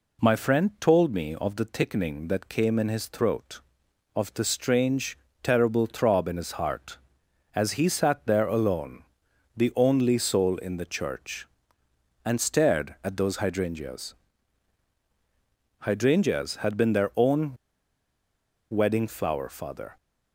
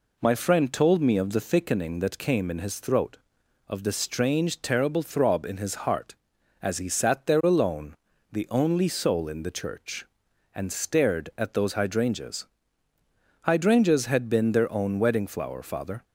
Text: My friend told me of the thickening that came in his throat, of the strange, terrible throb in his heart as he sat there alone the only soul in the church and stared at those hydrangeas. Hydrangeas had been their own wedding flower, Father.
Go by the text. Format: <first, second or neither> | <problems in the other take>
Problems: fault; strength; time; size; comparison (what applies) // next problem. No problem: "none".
second | pauses between "alone" and "the"; noticeable; at 9.0 s; 0.54 s long; also in the second // pauses between "own" and "wedding"; at 17.5 s; 1.1 s long